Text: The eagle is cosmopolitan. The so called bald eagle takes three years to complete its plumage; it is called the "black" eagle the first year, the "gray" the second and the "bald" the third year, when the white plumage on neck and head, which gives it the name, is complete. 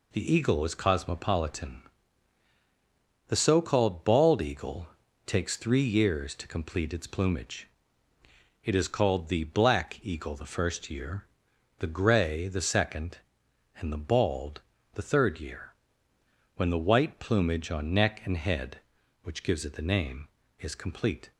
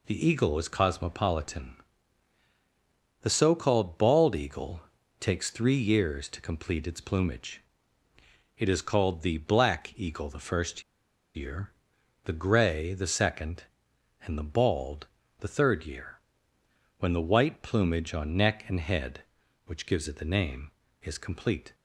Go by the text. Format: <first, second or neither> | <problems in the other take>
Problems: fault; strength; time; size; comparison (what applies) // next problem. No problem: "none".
first | pauses between "eagle" and "takes"; slight; at 4.8 s; 0.36 s long; slight in the first // pauses between "first" and "year"; noticeable; at 10.8 s; 0.53 s long // pauses between "bald" and "the"; slight; at 15.0 s; 0.34 s long; slight in the first